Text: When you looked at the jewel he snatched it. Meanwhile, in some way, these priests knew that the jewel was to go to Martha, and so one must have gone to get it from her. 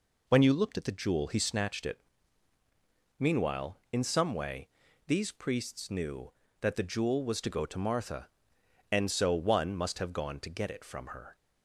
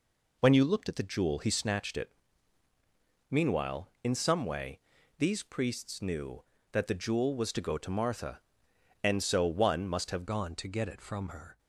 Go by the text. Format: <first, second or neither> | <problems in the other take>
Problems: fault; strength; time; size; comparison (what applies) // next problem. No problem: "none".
first | changes voice at "gone"; from 10.2 s on; 1.3 s long